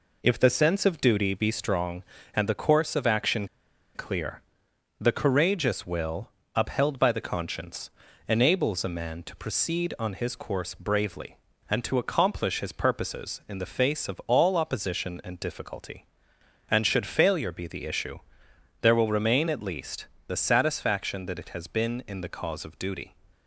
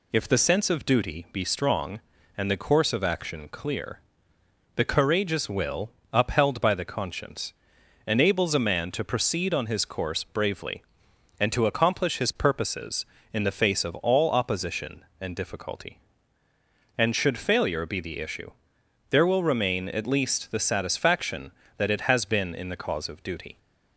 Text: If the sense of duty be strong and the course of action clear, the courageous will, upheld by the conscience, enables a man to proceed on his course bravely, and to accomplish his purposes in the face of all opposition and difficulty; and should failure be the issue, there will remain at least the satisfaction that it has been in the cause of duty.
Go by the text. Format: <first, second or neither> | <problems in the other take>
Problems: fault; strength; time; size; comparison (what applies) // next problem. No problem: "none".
second | pauses between "action" and "clear"; noticeable; at 3.4 s; 0.47 s long // pauses between "least" and "the"; slight; at 20.0 s; 0.22 s long